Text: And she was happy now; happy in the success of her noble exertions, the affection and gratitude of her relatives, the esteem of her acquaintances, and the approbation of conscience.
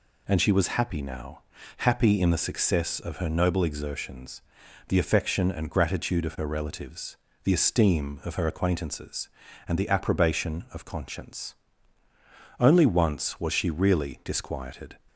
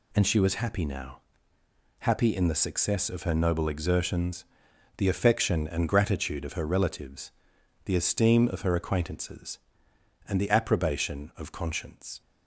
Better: second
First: goes on to say "Only once was she really disquieted"; strong; from 12.5 s on; 2.3 s long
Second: none

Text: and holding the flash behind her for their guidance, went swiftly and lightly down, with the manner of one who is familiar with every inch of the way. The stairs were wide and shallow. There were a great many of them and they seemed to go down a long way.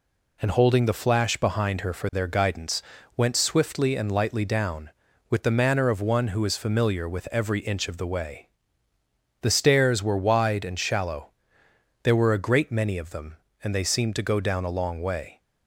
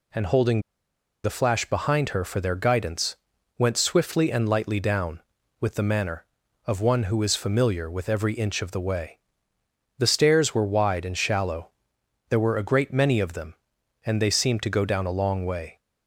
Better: first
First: none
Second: pauses between "holding" and "the"; noticeable; at 0.6 s; 0.63 s long

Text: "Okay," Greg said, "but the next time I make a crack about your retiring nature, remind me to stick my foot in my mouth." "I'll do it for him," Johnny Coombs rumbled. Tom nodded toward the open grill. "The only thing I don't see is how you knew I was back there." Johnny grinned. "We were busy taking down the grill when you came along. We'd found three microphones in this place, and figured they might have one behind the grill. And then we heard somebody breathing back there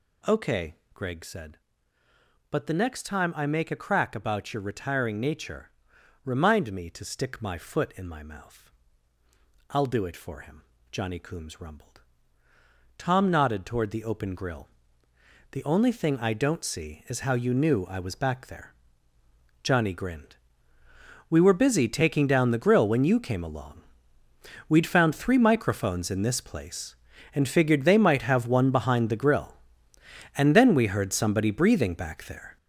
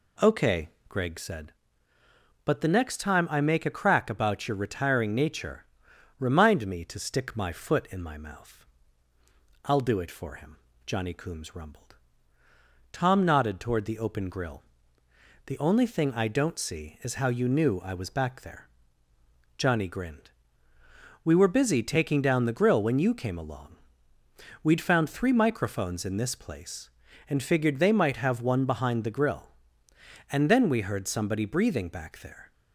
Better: second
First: gets louder; strong; throughout; 9 dB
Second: none

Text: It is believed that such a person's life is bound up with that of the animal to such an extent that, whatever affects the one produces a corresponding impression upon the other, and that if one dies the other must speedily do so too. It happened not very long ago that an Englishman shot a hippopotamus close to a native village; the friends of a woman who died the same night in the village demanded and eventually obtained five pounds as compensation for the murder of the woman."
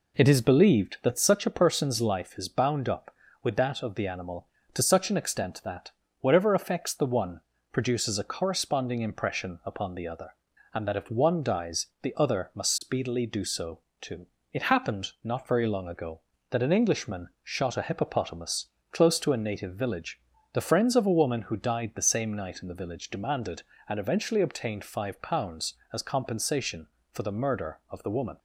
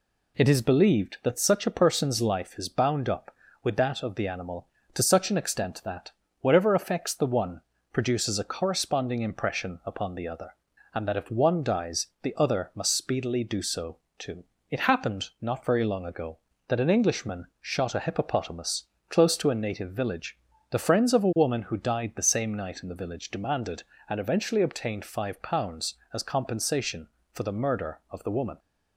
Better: second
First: starts louder than the rest; slight; until 1.5 s; 3.5 dB // pauses between "one" and "produces"; slight; at 7.4 s; 0.32 s long // pauses between "so" and "too"; slight; at 13.7 s; 0.22 s long // pauses between "Englishman" and "shot"; slight; at 17.2 s; 0.16 s long // pauses between "hippopotamus" and "close"; slight; at 18.6 s; 0.24 s long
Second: pauses between "one" and "produces"; slight; at 7.6 s; 0.32 s long // pauses between "so" and "too"; slight; at 13.9 s; 0.22 s long // pauses between "Englishman" and "shot"; slight; at 17.4 s; 0.16 s long // pauses between "hippopotamus" and "close"; slight; at 18.8 s; 0.24 s long

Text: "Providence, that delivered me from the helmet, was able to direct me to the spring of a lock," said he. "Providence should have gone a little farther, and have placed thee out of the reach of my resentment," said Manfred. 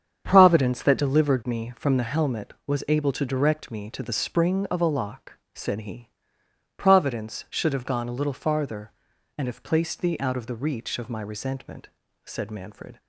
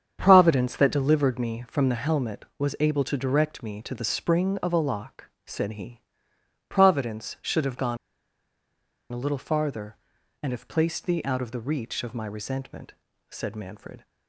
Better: first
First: starts louder than the rest; strong; until 1.2 s; 8 dB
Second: starts louder than the rest; strong; until 1.2 s; 8 dB // pauses between "gone" and "a"; at 7.9 s; 1.1 s long

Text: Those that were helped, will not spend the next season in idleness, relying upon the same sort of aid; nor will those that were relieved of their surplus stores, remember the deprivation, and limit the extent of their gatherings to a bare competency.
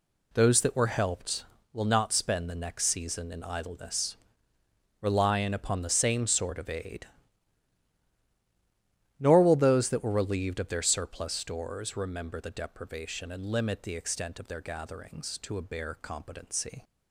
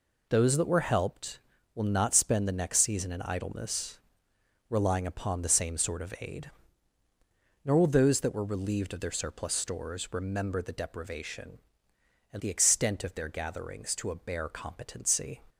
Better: first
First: none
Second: skips "limit"; at 12.4 s

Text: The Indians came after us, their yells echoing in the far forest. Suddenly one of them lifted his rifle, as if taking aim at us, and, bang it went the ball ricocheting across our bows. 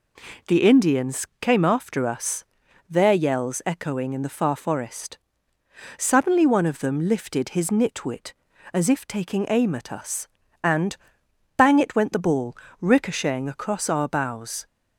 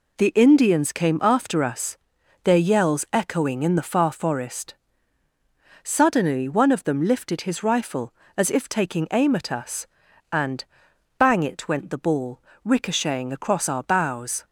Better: second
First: pauses between "Indians" and "came"; slight; at 1.2 s; 0.16 s long // says "nitwit" for "rifle"; at 7.7 s // pauses between "ball" and "ricocheting"; slight; at 12.5 s; 0.26 s long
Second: pauses between "ball" and "ricocheting"; slight; at 12.4 s; 0.22 s long

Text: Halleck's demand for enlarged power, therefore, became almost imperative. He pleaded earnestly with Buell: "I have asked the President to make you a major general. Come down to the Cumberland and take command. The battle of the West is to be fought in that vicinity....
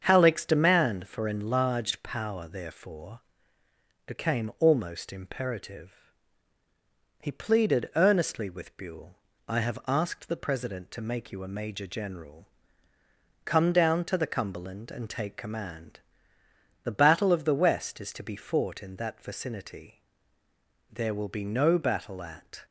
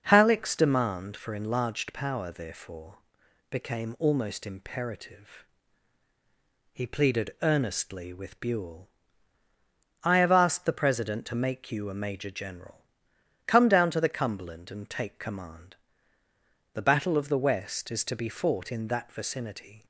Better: second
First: starts louder than the rest; strong; until 1.0 s; 7 dB // goes on to say "There will be no battle at"; strong; from 20.9 s on; 1.7 s long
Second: none

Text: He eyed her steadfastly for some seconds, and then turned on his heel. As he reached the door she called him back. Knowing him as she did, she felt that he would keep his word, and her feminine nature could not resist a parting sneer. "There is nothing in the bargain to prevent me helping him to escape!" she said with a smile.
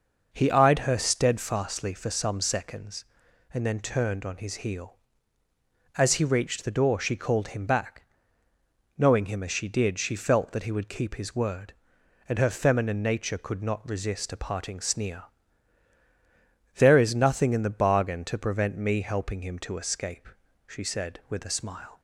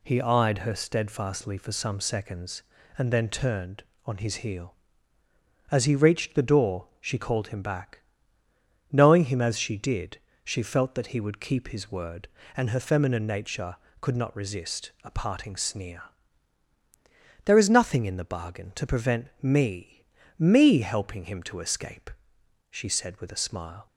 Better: first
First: none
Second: says "me" twice; at 20.3 s

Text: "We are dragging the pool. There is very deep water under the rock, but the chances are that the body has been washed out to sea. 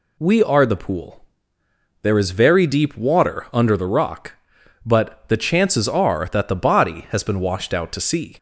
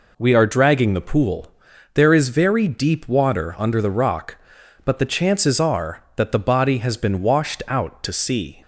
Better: second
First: skips "dragging"; at 0.6 s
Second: none

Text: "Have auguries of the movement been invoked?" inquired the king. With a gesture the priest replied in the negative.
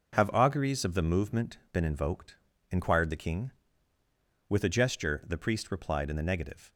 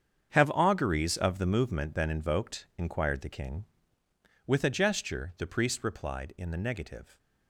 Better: first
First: none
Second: gets quieter; strong; throughout; 13.5 dB

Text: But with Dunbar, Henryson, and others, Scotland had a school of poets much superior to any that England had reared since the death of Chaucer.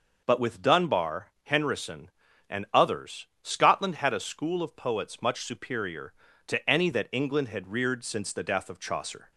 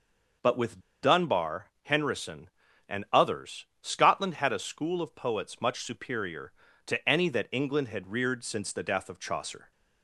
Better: first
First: none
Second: pauses between "with" and "Dunbar"; slight; at 0.7 s; 0.23 s long

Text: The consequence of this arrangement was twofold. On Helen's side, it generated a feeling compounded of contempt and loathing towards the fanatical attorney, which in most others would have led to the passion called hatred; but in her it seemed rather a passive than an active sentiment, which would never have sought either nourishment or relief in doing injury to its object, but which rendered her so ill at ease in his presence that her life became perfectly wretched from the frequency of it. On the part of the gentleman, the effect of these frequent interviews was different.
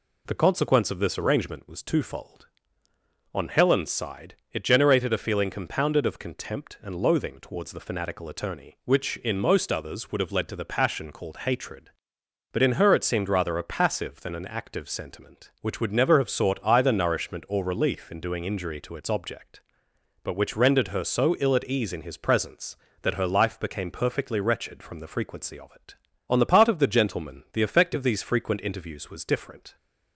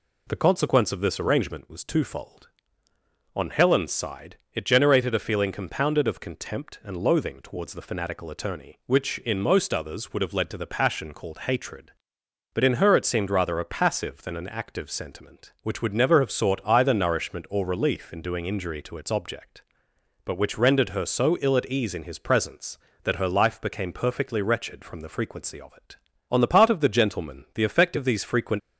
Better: first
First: none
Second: stops before "interviews was different"; at 28.5 s

